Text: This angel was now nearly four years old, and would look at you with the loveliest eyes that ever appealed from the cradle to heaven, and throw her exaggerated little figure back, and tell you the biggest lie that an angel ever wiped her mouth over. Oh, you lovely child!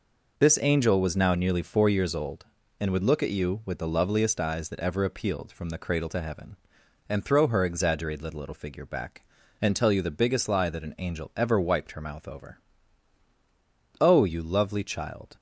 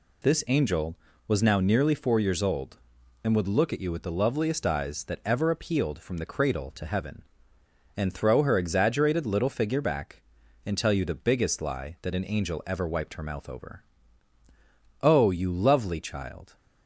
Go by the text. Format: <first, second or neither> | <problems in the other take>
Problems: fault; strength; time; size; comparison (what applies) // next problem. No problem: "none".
second | says "little" twice; at 8.3 s